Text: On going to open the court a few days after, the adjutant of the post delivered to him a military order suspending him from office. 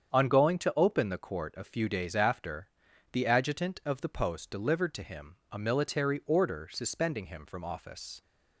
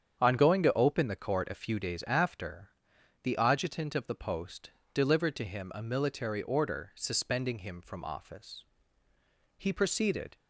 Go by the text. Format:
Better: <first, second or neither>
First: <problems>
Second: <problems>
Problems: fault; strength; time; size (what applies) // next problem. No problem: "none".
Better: first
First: starts louder than the rest; strong; until 1.1 s; 8 dB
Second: starts louder than the rest; strong; until 1.2 s; 8 dB // pauses between "post" and "delivered"; slight; at 4.7 s; 0.20 s long // goes on to say "He proceeded"; noticeable; from 9.5 s on; 0.78 s long